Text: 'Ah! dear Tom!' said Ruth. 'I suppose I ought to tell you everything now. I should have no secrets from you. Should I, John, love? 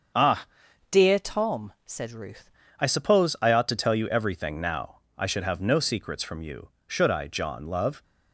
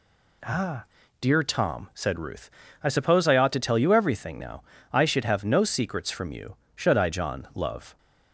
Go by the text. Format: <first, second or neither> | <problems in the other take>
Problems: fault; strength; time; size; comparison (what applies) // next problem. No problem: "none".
second | starts louder than the rest; until 1.6 s; 6.5 dB // changes voice from "dear" to "Ruth"; from 0.9 to 2.4 s; 1.5 s long